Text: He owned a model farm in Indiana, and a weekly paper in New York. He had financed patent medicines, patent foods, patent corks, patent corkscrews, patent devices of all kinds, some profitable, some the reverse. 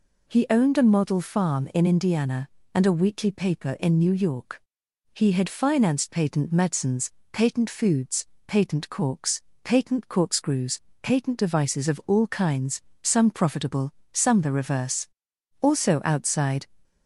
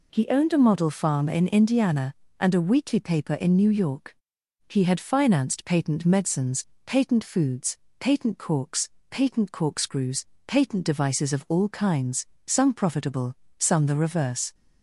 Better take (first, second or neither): second